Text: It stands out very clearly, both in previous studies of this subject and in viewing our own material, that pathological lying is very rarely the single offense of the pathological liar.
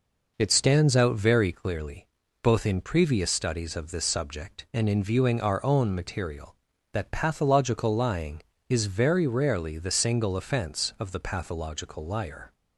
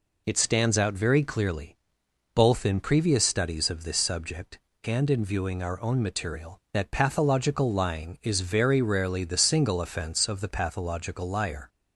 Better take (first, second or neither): neither